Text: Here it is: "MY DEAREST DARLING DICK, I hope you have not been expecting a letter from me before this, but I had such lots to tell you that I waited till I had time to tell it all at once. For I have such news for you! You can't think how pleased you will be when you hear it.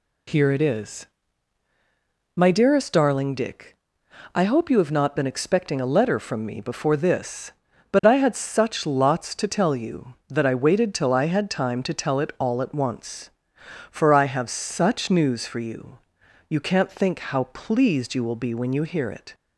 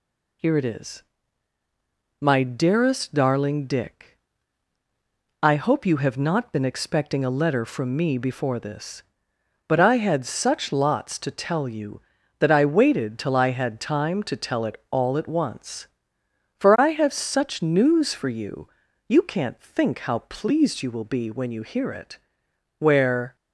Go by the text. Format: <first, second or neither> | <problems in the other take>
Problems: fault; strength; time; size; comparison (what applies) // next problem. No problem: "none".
first | goes on to say "Where"; from 22.7 s on; 0.56 s long